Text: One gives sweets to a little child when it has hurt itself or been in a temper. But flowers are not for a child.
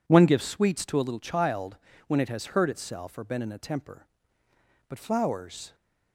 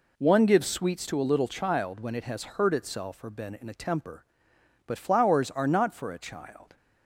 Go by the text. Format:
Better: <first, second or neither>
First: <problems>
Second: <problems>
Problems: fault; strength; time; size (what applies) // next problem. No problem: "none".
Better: second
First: pauses between "child" and "when"; slight; at 1.7 s; 0.28 s long // stops before "are not for a child"; at 5.7 s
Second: none